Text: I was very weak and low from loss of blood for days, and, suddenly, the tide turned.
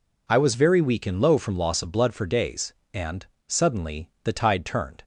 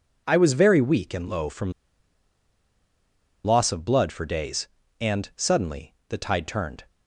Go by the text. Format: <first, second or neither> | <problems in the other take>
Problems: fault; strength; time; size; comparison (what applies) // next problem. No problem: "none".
first | pauses between "from" and "loss"; strong; at 1.7 s; 1.7 s long